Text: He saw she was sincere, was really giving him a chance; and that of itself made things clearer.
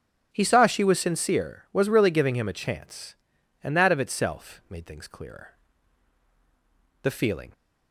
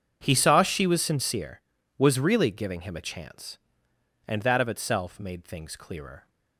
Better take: second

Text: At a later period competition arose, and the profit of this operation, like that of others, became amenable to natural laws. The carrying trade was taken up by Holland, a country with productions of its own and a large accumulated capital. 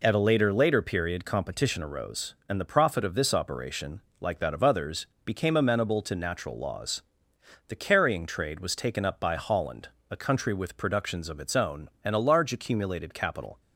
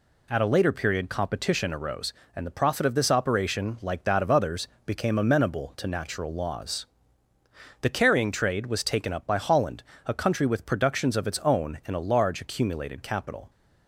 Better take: second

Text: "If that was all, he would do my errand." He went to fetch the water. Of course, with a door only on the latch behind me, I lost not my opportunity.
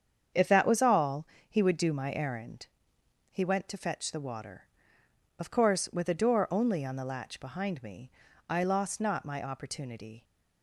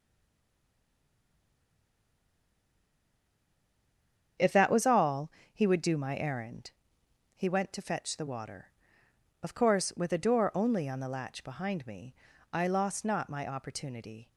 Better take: first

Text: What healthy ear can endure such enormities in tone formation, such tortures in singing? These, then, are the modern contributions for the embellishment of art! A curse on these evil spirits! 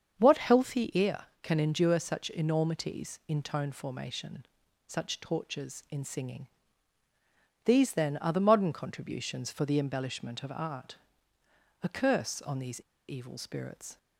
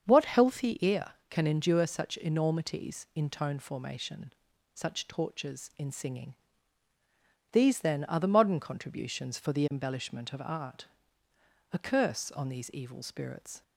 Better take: second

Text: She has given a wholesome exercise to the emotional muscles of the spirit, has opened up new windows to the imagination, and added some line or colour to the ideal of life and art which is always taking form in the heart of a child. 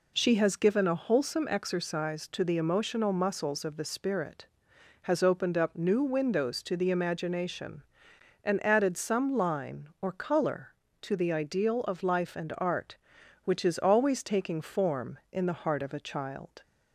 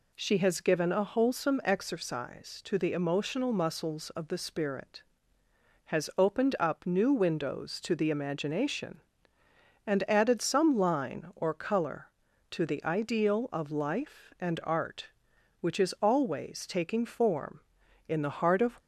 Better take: first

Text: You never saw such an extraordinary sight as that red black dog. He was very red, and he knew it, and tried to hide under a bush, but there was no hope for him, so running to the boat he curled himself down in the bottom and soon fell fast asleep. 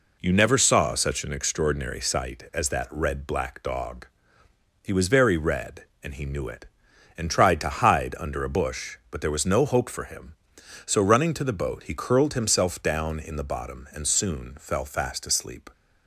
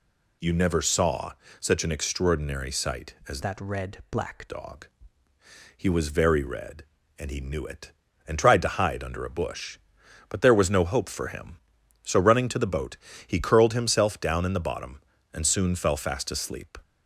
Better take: first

